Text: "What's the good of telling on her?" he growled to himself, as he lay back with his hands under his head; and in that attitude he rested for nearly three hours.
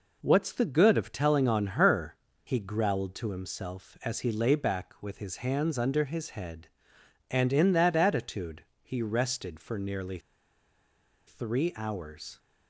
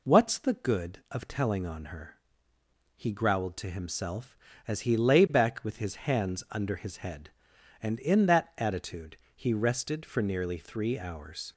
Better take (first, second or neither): second